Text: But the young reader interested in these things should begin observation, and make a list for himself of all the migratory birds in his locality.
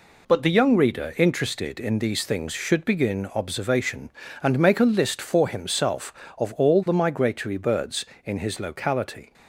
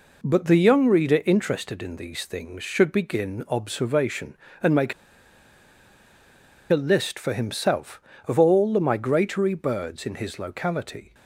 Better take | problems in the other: first | pauses between "make" and "a"; strong; at 4.9 s; 1.7 s long

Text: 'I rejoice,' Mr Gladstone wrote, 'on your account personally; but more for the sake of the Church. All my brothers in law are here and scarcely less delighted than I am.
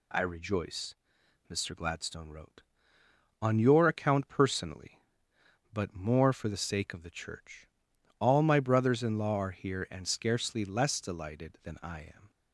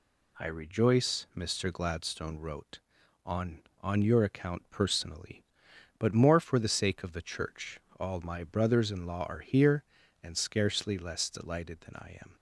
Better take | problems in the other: first | says "on" twice; at 3.8 s

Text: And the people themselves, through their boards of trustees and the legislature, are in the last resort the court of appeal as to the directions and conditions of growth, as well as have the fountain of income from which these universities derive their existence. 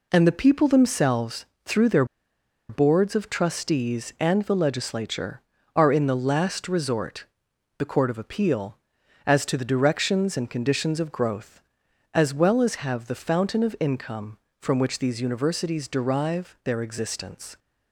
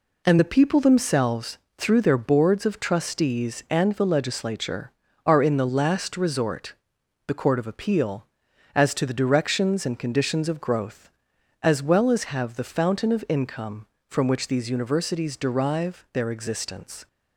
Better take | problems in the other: second | pauses between "their" and "boards"; noticeable; at 2.0 s; 0.65 s long // pauses between "resort" and "the"; noticeable; at 7.2 s; 0.54 s long; noticeable in the second

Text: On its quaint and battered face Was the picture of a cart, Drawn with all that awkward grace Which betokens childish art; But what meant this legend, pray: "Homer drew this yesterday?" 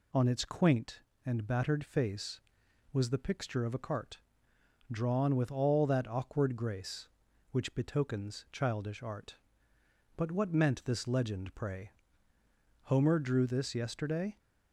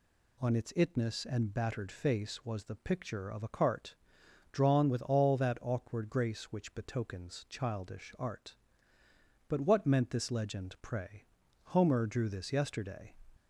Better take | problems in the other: first | says "itness" for "quaint"; at 0.7 s

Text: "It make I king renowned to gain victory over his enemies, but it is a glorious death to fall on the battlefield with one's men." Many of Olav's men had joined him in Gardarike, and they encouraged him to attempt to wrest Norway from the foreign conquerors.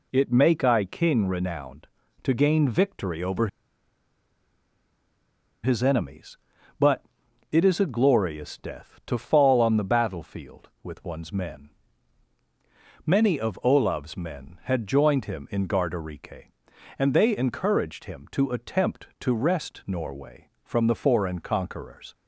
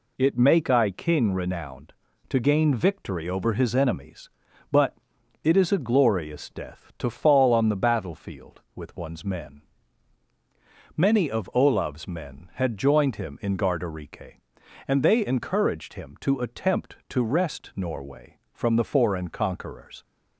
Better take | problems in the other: second | pauses between "over" and "his"; strong; at 3.4 s; 2.1 s long // pauses between "but" and "it"; noticeable; at 7.0 s; 0.46 s long; noticeable in the second

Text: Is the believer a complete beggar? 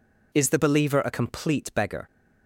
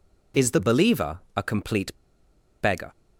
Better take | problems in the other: first | pauses between "complete" and "beggar"; noticeable; at 1.9 s; 0.64 s long

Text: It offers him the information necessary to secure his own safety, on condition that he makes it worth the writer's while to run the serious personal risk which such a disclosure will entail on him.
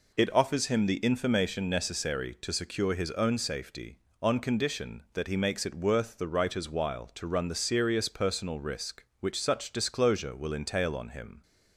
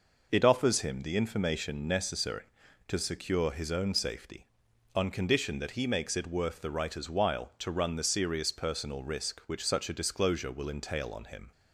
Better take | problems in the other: second | skips "a"; at 9.7 s

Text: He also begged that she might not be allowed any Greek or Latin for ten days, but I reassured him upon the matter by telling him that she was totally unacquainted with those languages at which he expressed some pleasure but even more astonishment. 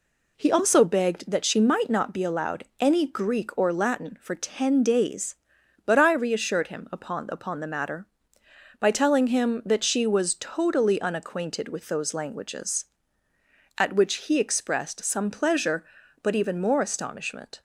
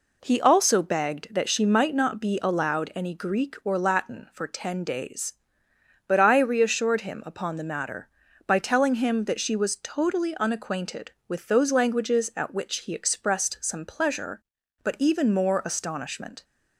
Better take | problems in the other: second | pauses between "allowed" and "any"; slight; at 2.6 s; 0.16 s long // says "upon" twice; at 7.2 s

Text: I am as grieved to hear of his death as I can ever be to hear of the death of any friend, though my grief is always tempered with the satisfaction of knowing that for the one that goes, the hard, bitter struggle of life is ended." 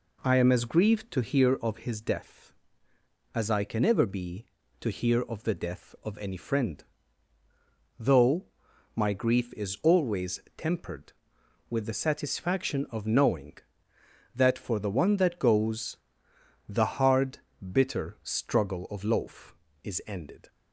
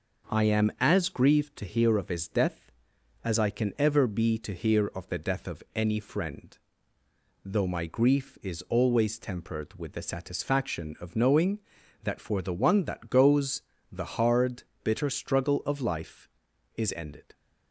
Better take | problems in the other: second | pauses between "though" and "my"; noticeable; at 8.4 s; 0.50 s long // pauses between "always" and "tempered"; slight; at 10.4 s; 0.16 s long // says "loaf" for "life"; at 19.0 s

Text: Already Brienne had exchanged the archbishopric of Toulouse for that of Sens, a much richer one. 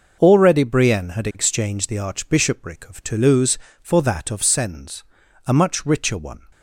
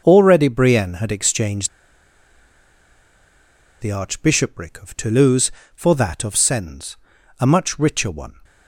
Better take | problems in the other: first | pauses between "exchanged" and "the"; strong; at 1.6 s; 2.1 s long

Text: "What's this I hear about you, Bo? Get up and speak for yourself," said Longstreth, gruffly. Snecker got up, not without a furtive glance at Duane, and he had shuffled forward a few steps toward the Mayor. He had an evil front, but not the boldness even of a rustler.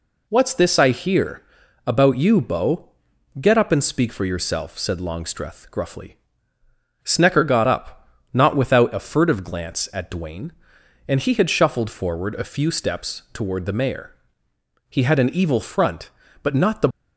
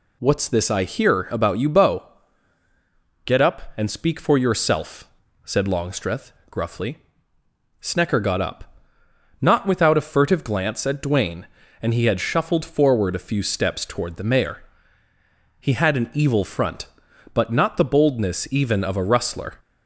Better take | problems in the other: second | pauses between "hear" and "about"; at 1.4 s; 0.42 s long // stops before "boldness even of a rustler"; at 16.9 s

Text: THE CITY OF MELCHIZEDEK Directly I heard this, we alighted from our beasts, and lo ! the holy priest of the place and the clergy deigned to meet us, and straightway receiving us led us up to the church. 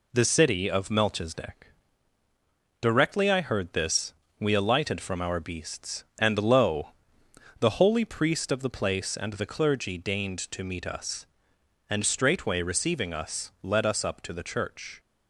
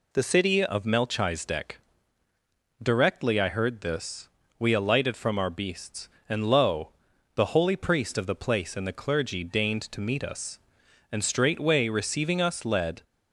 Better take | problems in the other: first | pauses between "MELCHIZEDEK" and "Directly"; at 1.7 s; 1.0 s long; also in the first // stops before "us up to the church"; at 13.0 s

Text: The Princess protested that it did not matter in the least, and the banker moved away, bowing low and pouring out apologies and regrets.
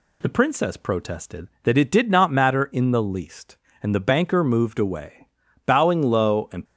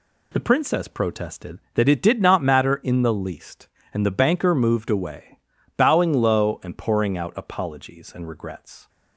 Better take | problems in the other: second | stops before "pouring out apologies and regrets"; at 6.6 s

